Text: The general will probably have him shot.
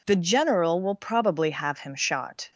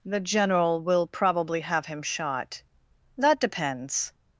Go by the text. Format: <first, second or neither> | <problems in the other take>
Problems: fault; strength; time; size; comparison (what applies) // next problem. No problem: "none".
first | goes on to say "That depends"; noticeable; from 3.1 s on; 0.96 s long